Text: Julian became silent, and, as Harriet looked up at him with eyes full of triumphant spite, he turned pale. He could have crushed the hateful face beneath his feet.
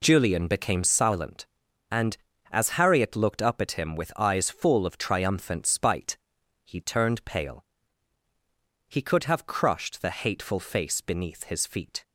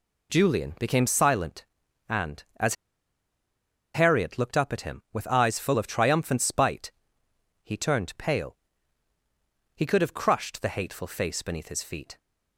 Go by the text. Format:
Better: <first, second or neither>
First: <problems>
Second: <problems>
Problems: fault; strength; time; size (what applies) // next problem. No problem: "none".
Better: first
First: none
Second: pauses between "as" and "Harriet"; at 2.7 s; 1.1 s long